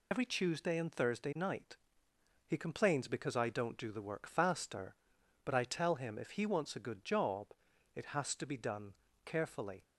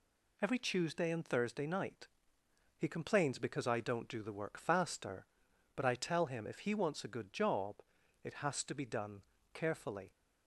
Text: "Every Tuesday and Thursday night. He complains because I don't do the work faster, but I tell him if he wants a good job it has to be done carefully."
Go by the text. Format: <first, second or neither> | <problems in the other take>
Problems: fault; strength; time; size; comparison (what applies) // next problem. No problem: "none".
second | loses the start of "Every"; at 0.1 s; 45 ms // pauses between "job" and "it"; noticeable; at 7.4 s; 0.48 s long; noticeable in the second // pauses between "done" and "carefully"; slight; at 8.9 s; 0.32 s long; slight in the second